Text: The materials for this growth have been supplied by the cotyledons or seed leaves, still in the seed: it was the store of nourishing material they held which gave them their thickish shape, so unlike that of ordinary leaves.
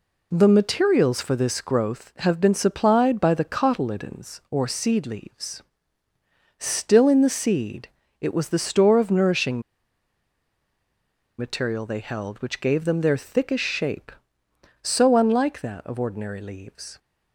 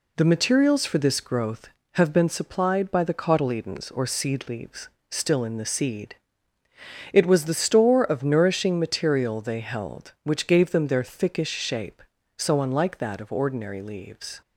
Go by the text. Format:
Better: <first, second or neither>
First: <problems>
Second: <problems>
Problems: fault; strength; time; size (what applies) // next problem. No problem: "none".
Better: second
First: pauses between "nourishing" and "material"; strong; at 9.6 s; 1.7 s long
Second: none